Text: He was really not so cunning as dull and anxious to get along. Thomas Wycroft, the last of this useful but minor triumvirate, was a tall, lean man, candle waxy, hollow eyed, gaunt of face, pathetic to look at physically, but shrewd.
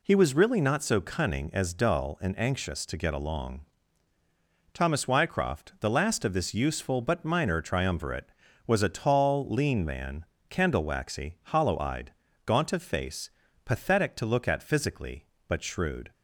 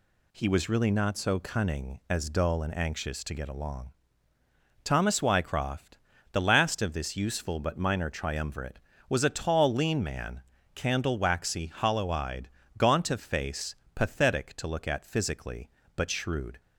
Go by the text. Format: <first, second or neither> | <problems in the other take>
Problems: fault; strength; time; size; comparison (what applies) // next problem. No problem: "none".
neither | none